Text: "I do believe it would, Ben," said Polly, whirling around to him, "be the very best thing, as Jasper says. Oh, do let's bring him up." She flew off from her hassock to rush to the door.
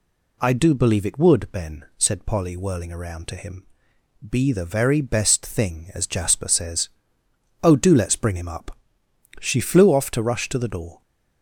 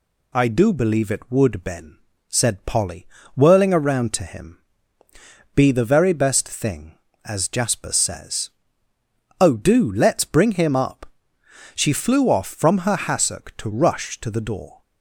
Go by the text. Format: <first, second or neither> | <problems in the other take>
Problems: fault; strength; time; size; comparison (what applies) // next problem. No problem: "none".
second | skips "from her hassock"; at 10.1 s